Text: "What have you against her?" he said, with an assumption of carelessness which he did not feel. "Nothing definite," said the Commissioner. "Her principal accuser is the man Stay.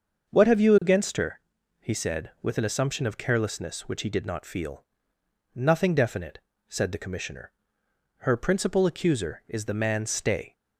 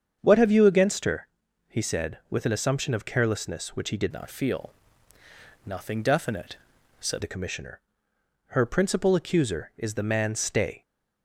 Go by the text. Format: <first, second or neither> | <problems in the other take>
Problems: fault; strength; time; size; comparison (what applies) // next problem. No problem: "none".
first | starts louder than the rest; strong; until 1.2 s; 7.5 dB; also in the first // changes voice from "not" to "said"; from 4.1 to 7.2 s; 3.1 s long